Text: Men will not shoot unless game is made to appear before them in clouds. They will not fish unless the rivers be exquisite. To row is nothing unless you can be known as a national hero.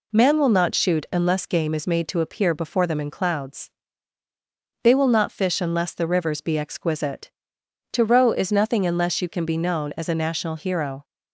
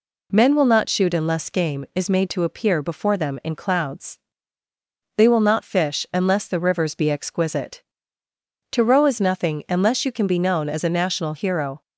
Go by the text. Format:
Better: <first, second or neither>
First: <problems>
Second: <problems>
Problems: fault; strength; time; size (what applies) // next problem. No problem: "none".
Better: second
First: says "Man" for "Men"; at 0.1 s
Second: none